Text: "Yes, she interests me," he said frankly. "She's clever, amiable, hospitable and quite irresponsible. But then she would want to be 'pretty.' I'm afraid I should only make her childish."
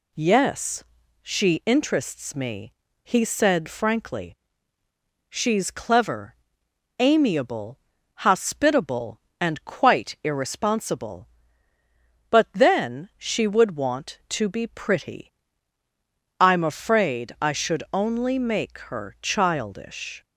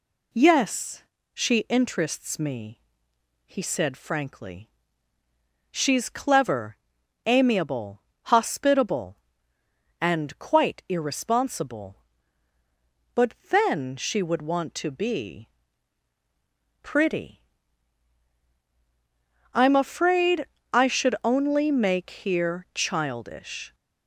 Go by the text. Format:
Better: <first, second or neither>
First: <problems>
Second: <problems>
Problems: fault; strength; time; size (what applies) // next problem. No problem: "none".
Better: first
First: none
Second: pauses between "But" and "then"; slight; at 13.3 s; 0.16 s long // pauses between "be" and "pretty"; strong; at 15.4 s; 1.3 s long // pauses between "afraid" and "I"; slight; at 20.4 s; 0.26 s long // says "here" for "her"; at 22.1 s